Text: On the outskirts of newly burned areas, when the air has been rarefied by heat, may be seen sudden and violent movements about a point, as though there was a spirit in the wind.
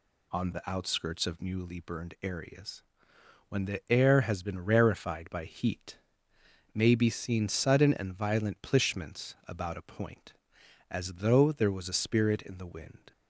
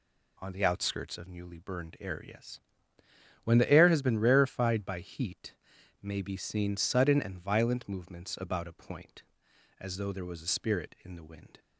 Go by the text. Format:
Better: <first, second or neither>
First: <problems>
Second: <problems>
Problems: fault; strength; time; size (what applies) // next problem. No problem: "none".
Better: second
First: says "plishments" for "movements"; at 8.5 s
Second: none